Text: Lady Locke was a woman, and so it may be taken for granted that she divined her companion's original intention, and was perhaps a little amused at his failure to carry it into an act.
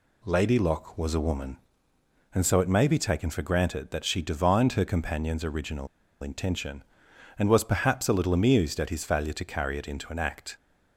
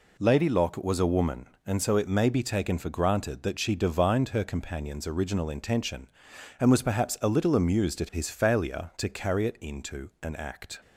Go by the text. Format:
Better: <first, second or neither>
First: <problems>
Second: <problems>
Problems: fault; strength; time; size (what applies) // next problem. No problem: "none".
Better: second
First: pauses between "original" and "intention"; slight; at 5.8 s; 0.35 s long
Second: none